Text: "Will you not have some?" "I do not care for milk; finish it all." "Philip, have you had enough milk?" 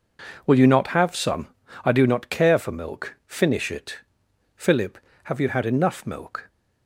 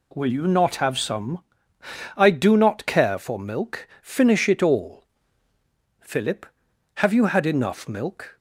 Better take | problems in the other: second | skips "all"; at 4.2 s

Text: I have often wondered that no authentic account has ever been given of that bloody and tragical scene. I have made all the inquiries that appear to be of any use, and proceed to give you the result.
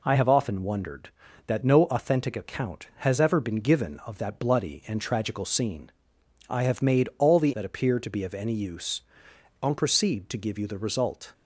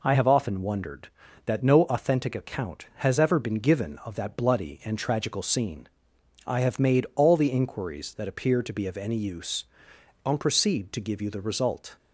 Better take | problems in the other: second | skips "inquiries"; at 7.5 s

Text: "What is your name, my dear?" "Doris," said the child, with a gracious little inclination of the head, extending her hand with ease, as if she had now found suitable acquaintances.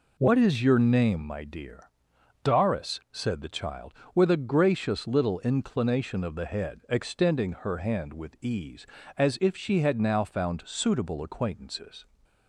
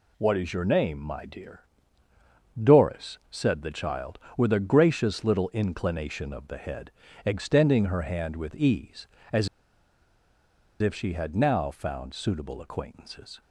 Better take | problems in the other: first | pauses between "as" and "if"; strong; at 9.4 s; 1.3 s long

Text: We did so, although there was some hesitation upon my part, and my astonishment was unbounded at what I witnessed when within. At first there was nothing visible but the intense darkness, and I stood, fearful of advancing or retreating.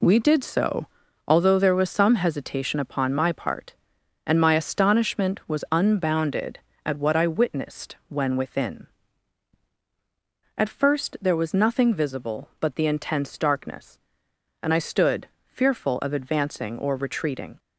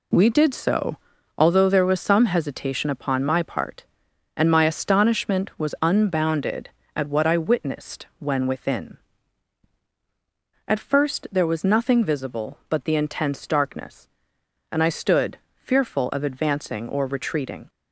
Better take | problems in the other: neither | none

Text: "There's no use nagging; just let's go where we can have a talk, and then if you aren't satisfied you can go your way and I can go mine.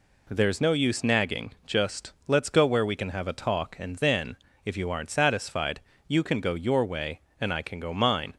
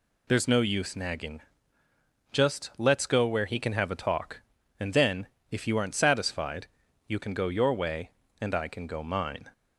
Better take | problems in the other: first | says "he" for "we"; at 3.4 s // pauses between "then" and "if"; slight; at 5.2 s; 0.24 s long; slight in the first // pauses between "satisfied" and "you"; at 6.6 s; 0.42 s long; slight in the first

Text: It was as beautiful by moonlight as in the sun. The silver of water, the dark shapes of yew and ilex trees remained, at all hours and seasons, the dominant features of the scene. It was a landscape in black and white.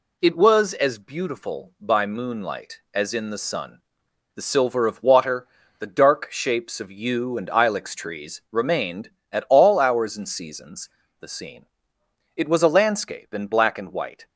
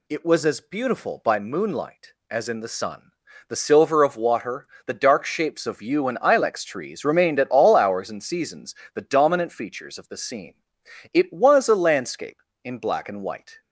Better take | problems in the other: second | skips "the dominant features of"; at 11.0 s

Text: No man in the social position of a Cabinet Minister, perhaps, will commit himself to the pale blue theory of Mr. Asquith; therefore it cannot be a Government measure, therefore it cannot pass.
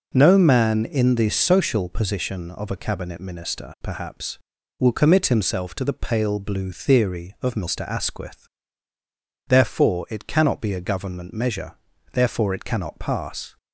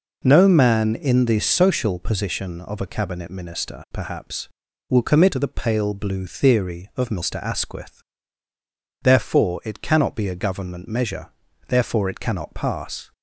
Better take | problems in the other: first | skips "himself"; at 5.3 s

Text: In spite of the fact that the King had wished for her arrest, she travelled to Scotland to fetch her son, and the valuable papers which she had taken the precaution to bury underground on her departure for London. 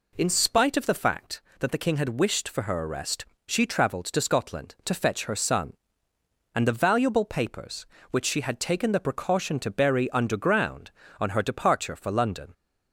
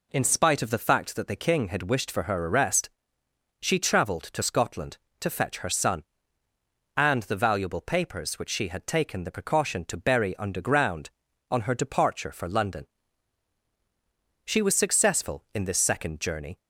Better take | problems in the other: first | goes on to say "She was successful in this second journey"; strong; from 14.4 s on; 2.1 s long

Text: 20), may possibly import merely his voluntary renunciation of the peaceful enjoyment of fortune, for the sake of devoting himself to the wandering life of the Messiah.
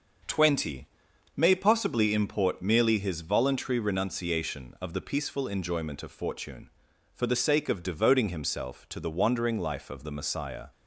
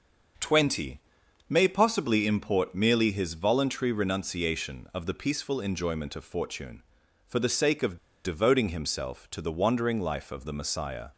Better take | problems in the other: first | starts louder than the rest; until 1.8 s; 6.5 dB; also in the first // pauses between "of" and "devoting"; slight; at 7.9 s; 0.28 s long

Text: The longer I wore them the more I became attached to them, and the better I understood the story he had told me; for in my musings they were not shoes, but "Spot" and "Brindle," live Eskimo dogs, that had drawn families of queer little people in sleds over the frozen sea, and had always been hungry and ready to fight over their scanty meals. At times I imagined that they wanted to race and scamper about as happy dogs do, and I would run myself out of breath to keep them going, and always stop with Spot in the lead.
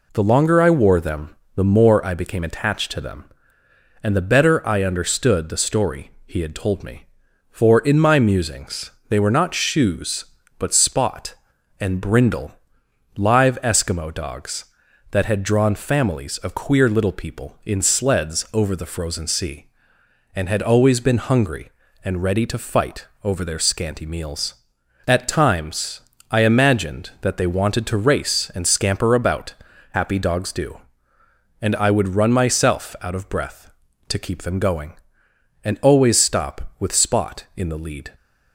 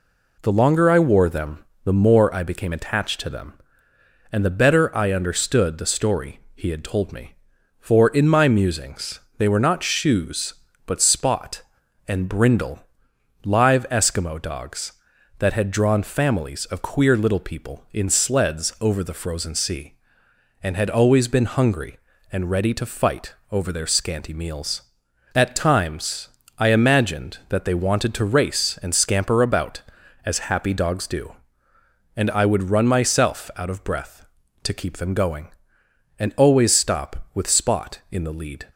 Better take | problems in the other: second | pauses between "them" and "the"; slight; at 1.3 s; 0.20 s long; slight in the second // pauses between "musings" and "they"; slight; at 8.8 s; 0.20 s long; slight in the second // pauses between "fight" and "over"; slight; at 23.0 s; 0.18 s long; slight in the second // pauses between "times" and "I"; slight; at 25.9 s; 0.30 s long; slight in the second // skips "as"; at 29.7 s

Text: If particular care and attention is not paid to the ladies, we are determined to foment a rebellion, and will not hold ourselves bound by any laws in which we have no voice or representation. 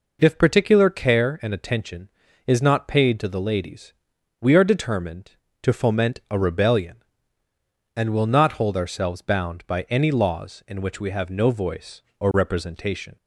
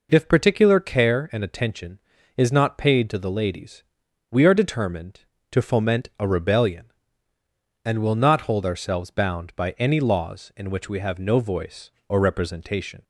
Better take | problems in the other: neither | none

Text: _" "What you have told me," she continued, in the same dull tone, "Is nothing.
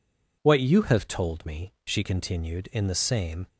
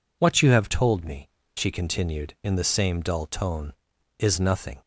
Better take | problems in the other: second | stops before "dull tone Is nothing"; at 3.4 s

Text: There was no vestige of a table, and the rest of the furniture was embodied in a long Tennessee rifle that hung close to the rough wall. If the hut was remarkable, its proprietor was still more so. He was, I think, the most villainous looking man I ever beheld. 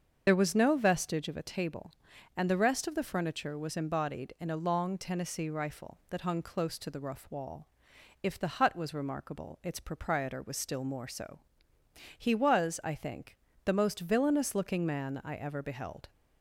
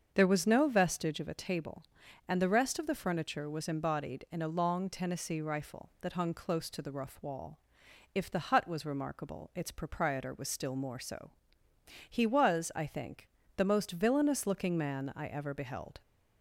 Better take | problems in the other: second | loses the start of "There"; at 0.2 s; 55 ms // starts louder than the rest; until 1.2 s; 6.5 dB; also in the second

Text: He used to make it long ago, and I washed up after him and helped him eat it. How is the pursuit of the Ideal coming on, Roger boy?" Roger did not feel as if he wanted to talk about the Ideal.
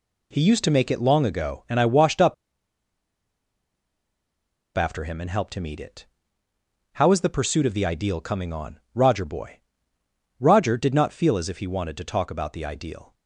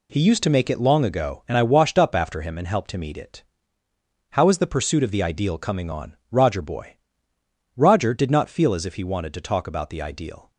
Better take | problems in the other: second | pauses between "up" and "after"; strong; at 2.3 s; 2.4 s long

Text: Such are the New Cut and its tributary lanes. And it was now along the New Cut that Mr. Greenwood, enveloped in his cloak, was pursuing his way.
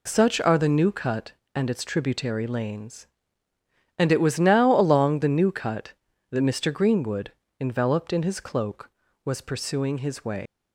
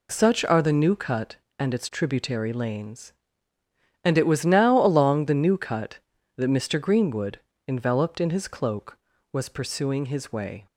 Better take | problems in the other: second | leaves "way" unfinished; at 10.4 s; 130 ms

